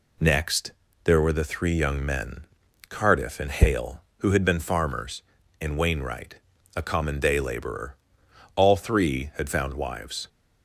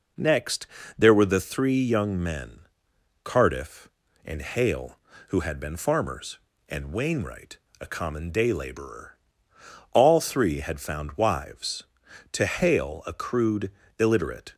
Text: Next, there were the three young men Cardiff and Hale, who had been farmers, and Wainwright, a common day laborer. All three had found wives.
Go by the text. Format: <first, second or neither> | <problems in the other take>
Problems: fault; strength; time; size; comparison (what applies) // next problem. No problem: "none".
first | pauses between "men" and "Cardiff"; noticeable; at 2.6 s; 0.64 s long; also in the first // goes on to say "To Hale a crude illiterate"; strong; from 12.3 s on; 2.2 s long